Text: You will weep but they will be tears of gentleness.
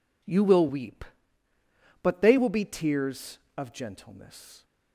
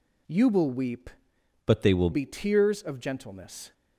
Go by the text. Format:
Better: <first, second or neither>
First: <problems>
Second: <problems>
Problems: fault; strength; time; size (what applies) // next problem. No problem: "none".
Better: first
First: none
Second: changes voice from "but" to "will"; from 1.6 to 2.0 s; 0.4 s long